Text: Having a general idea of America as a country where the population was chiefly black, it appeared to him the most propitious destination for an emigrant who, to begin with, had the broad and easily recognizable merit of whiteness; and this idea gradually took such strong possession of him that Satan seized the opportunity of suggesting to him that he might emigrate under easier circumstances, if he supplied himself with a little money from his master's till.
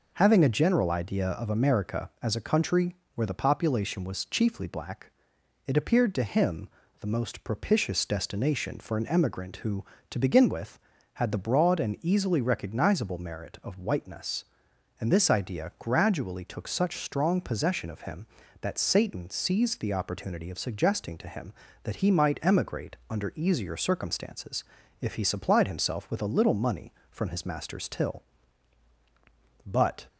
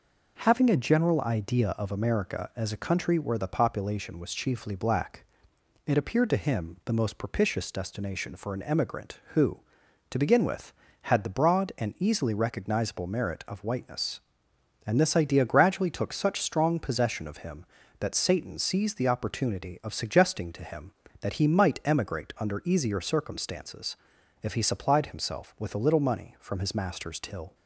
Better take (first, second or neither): second